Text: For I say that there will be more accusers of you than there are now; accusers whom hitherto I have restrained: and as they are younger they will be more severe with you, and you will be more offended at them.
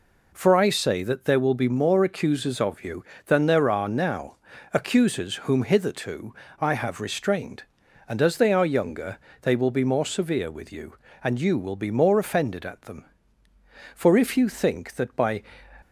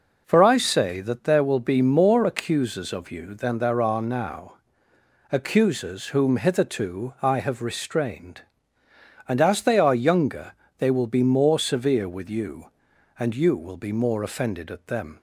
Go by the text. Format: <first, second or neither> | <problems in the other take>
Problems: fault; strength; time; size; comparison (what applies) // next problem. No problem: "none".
second | pauses between "hitherto" and "I"; slight; at 6.3 s; 0.26 s long // pauses between "younger" and "they"; slight; at 9.1 s; 0.22 s long; slight in the second // goes on to say "For if you think that by"; from 13.9 s on; 1.5 s long